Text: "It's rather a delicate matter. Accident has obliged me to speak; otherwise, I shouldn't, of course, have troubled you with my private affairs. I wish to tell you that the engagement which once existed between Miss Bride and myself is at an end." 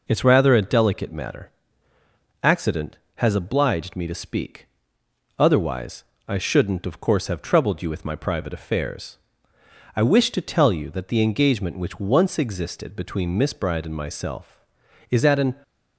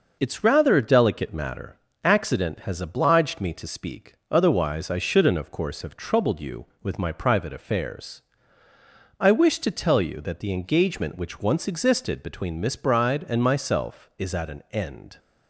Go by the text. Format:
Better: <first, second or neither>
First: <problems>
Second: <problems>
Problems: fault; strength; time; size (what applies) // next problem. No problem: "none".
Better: second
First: stops before "end"; at 15.6 s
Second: none